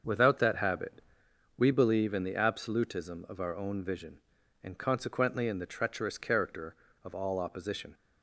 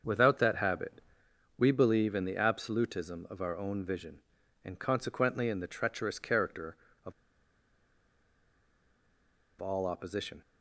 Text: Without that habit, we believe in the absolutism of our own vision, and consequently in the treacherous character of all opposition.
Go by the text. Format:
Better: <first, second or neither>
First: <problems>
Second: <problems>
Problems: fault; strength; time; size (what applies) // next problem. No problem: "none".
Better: first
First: starts louder than the rest; until 1.6 s; 6.5 dB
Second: starts louder than the rest; until 1.6 s; 6.5 dB // pauses between "of" and "all"; strong; at 7.1 s; 2.4 s long